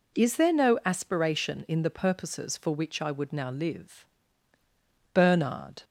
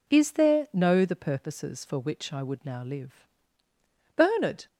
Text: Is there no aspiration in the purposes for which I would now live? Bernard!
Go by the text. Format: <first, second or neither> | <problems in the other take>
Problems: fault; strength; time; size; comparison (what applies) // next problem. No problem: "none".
first | skips "aspiration in"; at 1.0 s